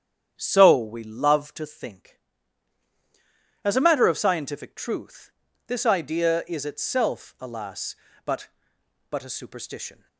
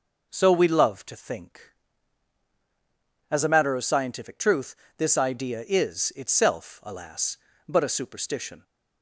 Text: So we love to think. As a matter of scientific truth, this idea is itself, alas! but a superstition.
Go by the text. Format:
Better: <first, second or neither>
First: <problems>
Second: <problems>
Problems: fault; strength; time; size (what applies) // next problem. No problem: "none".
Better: second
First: starts louder than the rest; strong; until 1.3 s; 9 dB // says "but" twice; at 9.0 s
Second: none